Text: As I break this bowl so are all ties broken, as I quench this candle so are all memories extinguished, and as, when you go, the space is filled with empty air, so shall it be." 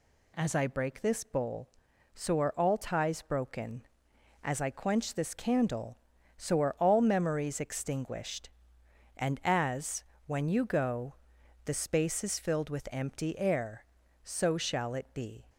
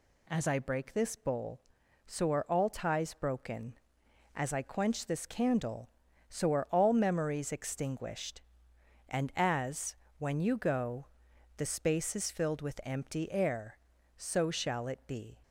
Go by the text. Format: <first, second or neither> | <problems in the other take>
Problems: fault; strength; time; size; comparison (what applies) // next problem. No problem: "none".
neither | none